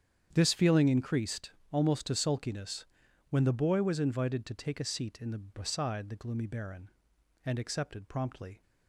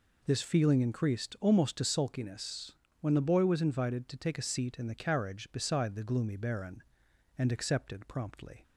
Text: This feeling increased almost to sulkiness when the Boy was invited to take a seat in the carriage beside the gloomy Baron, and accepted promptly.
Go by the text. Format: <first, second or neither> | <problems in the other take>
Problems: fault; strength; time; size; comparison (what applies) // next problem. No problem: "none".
second | starts louder than the rest; strong; until 1.3 s; 8.5 dB // pauses between "increased" and "almost"; slight; at 1.5 s; 0.20 s long // pauses between "sulkiness" and "when"; noticeable; at 2.8 s; 0.46 s long; slight in the second // skips "carriage"; at 5.3 s